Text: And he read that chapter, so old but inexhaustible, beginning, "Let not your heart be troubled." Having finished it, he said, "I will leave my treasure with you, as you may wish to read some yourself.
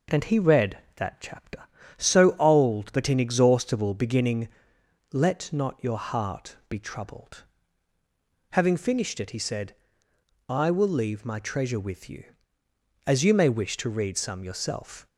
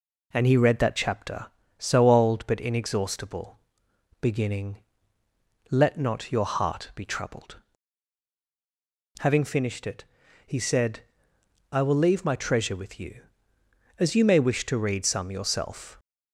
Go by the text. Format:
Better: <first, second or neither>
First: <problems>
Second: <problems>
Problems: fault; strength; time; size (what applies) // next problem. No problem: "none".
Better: neither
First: none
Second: none